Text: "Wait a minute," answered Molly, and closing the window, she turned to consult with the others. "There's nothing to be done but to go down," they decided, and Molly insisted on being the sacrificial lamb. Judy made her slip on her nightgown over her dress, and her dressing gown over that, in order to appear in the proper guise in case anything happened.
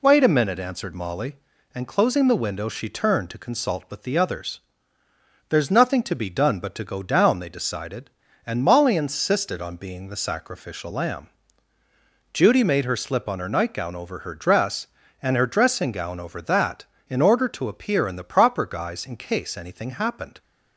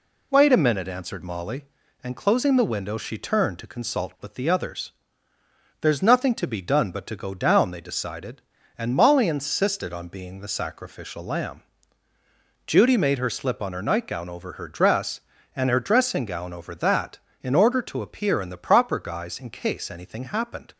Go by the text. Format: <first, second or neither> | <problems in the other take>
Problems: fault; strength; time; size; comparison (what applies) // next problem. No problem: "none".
neither | none